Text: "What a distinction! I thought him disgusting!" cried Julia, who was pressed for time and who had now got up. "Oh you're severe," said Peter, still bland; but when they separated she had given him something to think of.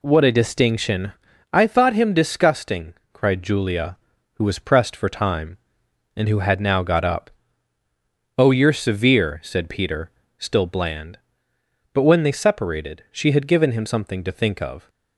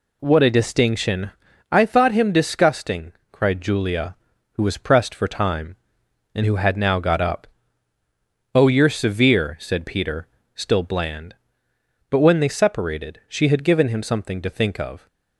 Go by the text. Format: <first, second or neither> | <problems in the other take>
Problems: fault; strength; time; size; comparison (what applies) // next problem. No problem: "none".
neither | none